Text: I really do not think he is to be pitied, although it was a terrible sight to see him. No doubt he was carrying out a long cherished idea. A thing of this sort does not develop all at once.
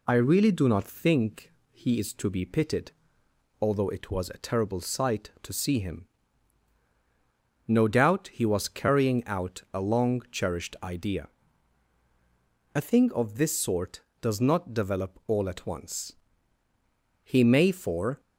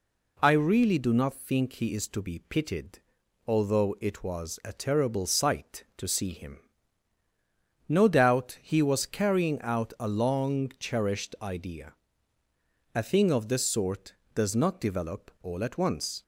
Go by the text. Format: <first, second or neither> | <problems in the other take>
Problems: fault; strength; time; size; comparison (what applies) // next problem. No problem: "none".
second | pauses between "think" and "he"; slight; at 1.5 s; 0.20 s long // goes on to say "He may for"; noticeable; from 17.2 s on; 0.98 s long